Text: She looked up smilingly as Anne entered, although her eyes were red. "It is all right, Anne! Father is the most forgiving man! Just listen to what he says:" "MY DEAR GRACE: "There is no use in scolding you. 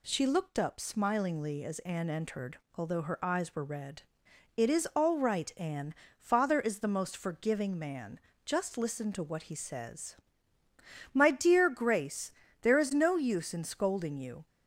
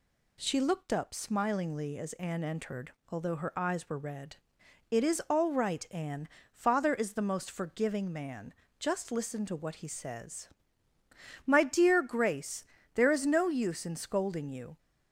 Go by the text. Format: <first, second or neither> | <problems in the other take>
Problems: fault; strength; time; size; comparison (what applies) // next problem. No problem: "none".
neither | none